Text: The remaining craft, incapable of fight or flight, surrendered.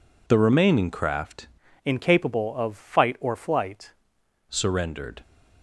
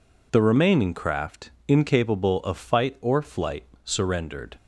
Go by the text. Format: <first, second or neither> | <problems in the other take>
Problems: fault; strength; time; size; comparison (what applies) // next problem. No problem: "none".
second | changes voice from "incapable" to "flight"; from 1.8 to 3.9 s; 2.1 s long